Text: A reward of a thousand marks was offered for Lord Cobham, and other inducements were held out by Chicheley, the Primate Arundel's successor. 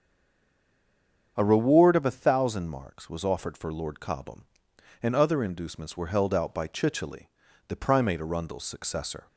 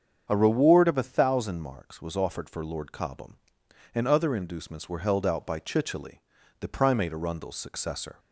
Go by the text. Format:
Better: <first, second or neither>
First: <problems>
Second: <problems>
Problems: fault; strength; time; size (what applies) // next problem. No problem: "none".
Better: second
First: stays silent before the first word; noticeable; until 1.3 s; 1.3 s long // starts louder than the rest; strong; until 2.3 s; 7.5 dB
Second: starts louder than the rest; strong; until 1.2 s; 7.5 dB